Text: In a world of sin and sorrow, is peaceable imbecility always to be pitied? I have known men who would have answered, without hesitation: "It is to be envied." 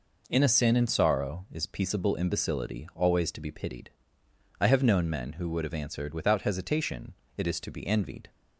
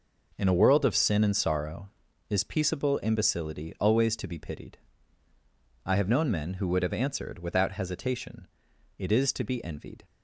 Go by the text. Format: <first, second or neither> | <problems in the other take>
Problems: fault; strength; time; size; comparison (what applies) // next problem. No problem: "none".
second | skips "world of"; at 0.4 s